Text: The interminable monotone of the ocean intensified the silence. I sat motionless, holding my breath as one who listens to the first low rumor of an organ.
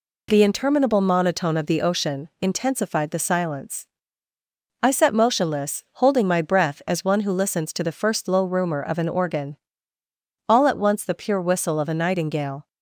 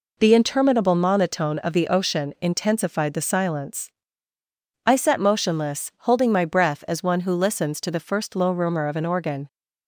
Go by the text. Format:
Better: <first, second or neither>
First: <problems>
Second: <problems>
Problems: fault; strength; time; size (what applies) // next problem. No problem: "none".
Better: second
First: goes on to say "All at once the pure whistle of a nightingale"; strong; from 10.4 s on; 2.2 s long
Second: none